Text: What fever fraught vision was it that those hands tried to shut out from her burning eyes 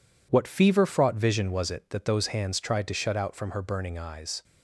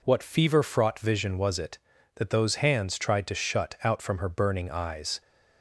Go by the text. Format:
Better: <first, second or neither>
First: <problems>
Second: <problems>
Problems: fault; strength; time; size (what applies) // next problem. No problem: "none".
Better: second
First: gets quieter; strong; throughout; 7 dB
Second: none